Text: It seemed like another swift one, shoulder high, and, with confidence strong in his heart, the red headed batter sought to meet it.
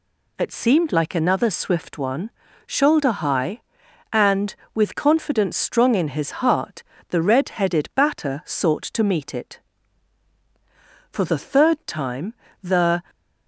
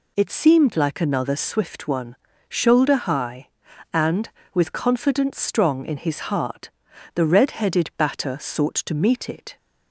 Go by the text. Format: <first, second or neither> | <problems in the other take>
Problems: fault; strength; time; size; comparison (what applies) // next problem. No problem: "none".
second | goes on to say "For the third time the"; strong; from 11.0 s on; 1.9 s long